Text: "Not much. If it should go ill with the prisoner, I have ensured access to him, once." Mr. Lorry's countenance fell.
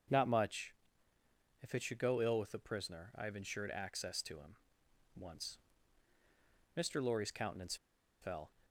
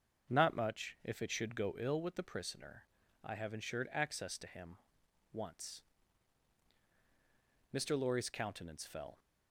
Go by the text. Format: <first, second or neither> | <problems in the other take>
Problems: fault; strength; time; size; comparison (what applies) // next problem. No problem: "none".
second | starts louder than the rest; until 1.9 s; 6.5 dB; also in the second // pauses between "countenance" and "fell"; noticeable; at 7.7 s; 0.46 s long